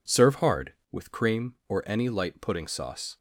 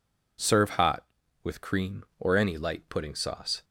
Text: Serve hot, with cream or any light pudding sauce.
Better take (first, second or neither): second